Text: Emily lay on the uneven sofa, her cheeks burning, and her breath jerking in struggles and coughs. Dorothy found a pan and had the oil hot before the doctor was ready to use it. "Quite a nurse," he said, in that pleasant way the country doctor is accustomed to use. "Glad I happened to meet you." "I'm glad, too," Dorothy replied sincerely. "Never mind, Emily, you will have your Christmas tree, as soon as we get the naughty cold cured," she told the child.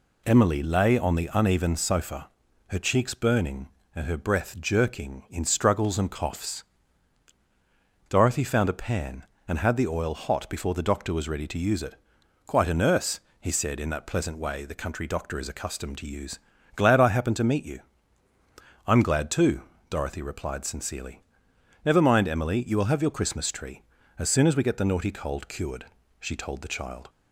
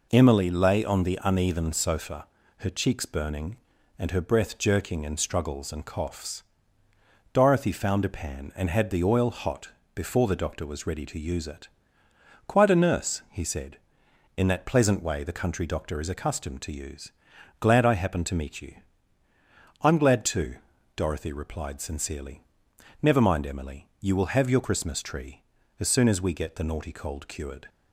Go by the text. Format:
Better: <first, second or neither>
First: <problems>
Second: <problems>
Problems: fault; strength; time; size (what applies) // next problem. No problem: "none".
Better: first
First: none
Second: pauses between "hot" and "before"; slight; at 9.6 s; 0.26 s long // stops before "she told the child"; at 27.6 s